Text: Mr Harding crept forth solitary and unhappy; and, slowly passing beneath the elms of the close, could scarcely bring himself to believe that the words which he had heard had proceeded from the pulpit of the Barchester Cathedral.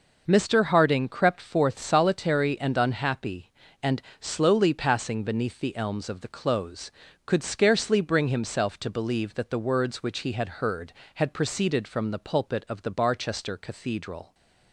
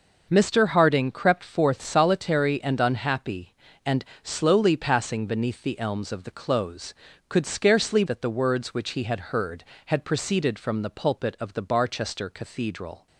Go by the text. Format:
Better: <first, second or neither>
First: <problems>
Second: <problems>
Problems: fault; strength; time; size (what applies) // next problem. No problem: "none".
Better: first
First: none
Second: skips "bring himself to believe"; at 8.0 s